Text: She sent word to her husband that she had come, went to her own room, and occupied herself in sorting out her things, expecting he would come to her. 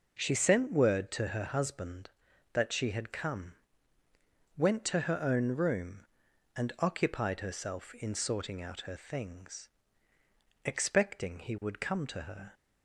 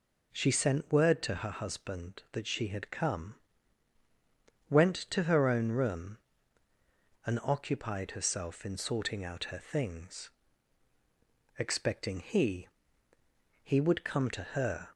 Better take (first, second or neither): first